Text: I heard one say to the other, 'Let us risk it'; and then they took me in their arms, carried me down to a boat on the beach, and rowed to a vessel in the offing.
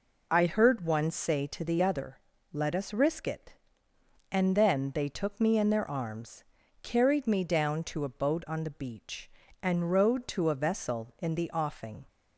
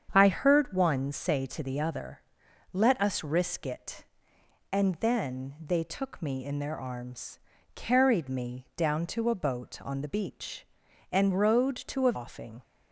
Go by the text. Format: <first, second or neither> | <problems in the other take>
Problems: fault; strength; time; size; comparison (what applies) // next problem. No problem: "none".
first | starts louder than the rest; strong; until 1.1 s; 8 dB // skips "vessel in the"; at 12.1 s